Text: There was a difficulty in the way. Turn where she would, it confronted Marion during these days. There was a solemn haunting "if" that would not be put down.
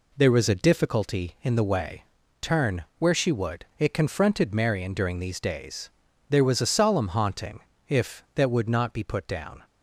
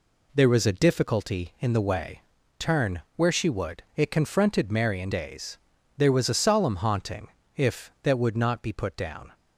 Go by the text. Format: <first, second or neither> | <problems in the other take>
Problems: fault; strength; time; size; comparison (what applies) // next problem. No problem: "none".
first | skips "during these"; at 5.1 s // pauses between "haunting" and "if"; slight; at 7.2 s; 0.28 s long; slight in the first